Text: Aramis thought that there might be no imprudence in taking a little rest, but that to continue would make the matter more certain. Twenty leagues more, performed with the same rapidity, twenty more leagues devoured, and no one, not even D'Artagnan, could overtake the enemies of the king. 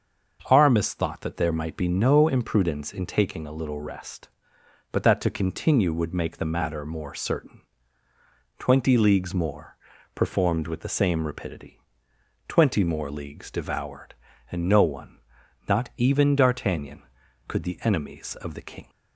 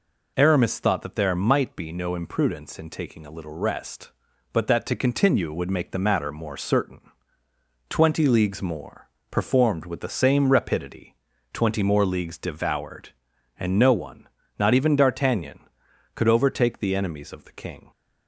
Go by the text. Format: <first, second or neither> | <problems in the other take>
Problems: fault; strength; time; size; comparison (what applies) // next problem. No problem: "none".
second | starts louder than the rest; until 1.4 s; 6.5 dB // skips "overtake"; at 17.6 s